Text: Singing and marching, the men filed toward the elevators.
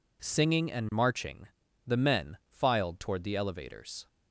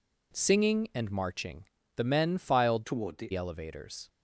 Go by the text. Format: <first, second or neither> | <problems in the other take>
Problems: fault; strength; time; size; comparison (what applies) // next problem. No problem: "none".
first | changes voice from "toward" to "the"; from 2.8 to 3.3 s; 0.5 s long